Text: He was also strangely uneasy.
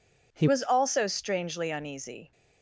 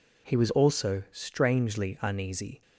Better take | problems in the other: second | changes voice at "was"; from 0.4 s on; 1.9 s long

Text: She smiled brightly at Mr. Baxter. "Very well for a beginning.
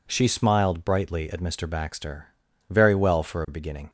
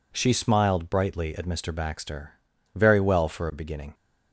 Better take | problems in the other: neither | none

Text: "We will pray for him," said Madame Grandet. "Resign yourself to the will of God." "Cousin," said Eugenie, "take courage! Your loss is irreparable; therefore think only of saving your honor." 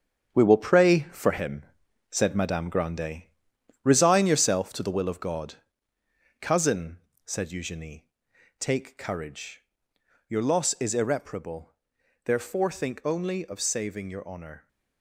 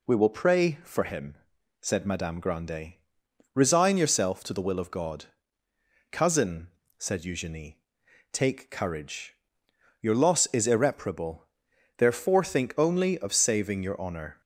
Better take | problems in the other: second | gets quieter; strong; throughout; 8 dB

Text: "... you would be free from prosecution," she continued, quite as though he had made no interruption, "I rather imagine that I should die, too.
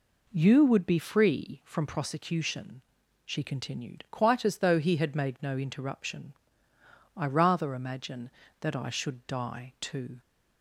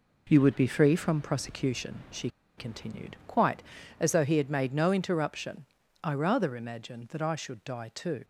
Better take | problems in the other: first | pauses between "she" and "continued"; slight; at 2.2 s; 0.29 s long

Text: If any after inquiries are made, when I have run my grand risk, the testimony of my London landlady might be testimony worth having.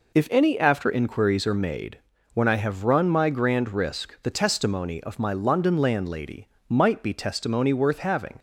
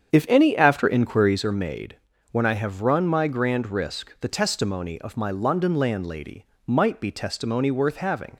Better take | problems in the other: first | starts louder than the rest; strong; until 1.4 s; 8 dB // pauses between "landlady" and "might"; slight; at 6.4 s; 0.20 s long; slight in the first

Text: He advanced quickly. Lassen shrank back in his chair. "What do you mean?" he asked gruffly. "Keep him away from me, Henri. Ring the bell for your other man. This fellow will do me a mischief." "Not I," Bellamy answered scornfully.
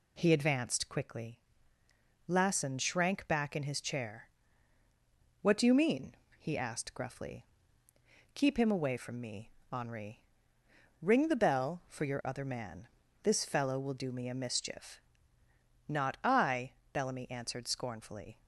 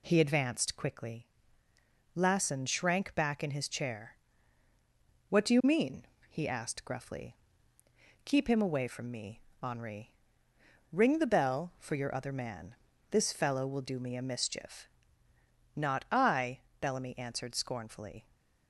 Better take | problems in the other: neither | none

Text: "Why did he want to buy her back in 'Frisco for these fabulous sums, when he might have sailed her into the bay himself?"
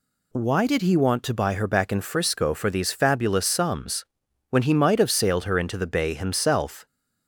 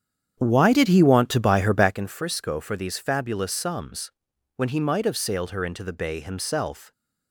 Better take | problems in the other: first | starts louder than the rest; strong; until 1.9 s; 9 dB

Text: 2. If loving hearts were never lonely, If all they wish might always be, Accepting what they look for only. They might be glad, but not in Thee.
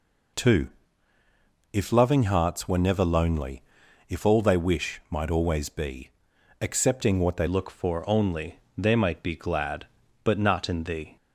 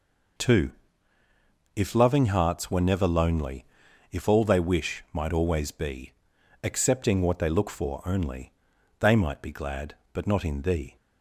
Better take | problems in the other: second | changes voice at "look"; from 7.4 s on; 3.7 s long

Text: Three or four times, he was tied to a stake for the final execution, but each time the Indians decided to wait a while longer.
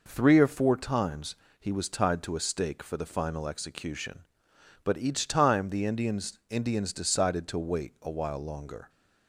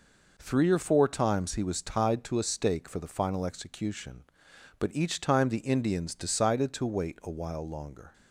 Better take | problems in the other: second | says "Indians" twice; at 6.4 s

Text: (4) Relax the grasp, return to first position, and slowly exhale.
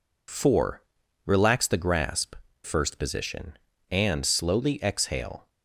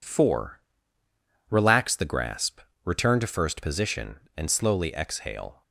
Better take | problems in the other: second | skips "return to"; at 2.4 s

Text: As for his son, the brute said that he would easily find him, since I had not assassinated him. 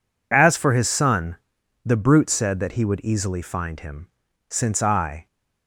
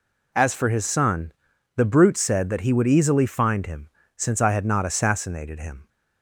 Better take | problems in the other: second | stops before "had not assassinated him"; at 5.2 s

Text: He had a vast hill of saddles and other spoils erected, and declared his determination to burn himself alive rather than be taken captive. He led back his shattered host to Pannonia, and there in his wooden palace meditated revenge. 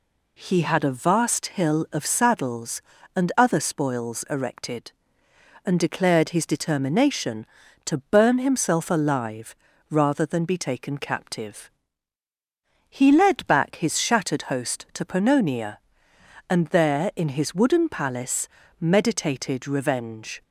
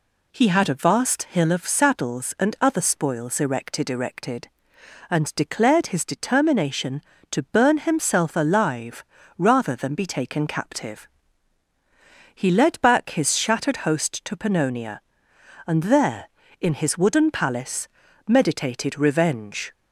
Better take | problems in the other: first | says "erected" twice; at 3.8 s // pauses between "alive" and "rather"; slight; at 9.0 s; 0.34 s long; slight in the first // pauses between "palace" and "meditated"; at 17.8 s; 0.40 s long; slight in the first

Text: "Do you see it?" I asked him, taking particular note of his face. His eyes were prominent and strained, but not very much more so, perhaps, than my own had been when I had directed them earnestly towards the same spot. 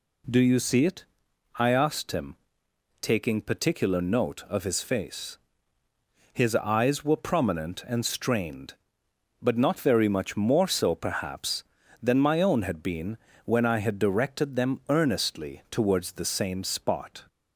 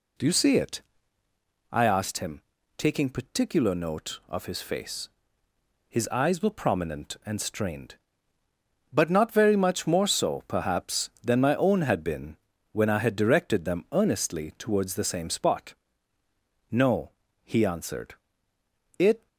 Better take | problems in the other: first | pauses between "been" and "when"; slight; at 12.3 s; 0.36 s long; slight in the first // goes on to say "No he answered It"; strong; from 16.7 s on; 2.5 s long

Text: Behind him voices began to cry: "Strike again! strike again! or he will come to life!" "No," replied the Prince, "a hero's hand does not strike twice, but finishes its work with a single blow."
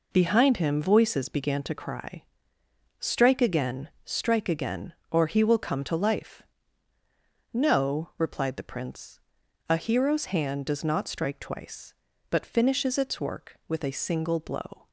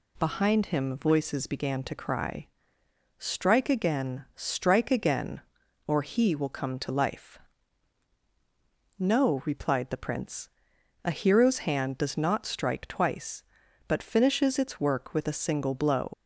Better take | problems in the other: first | leaves "blow" unfinished; at 16.1 s; 85 ms

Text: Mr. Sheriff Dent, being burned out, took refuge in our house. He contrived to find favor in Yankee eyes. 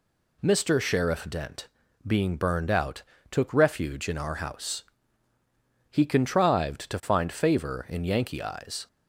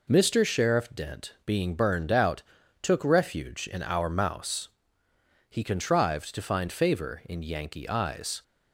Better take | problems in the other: first | says "mouse" for "house"; at 4.0 s

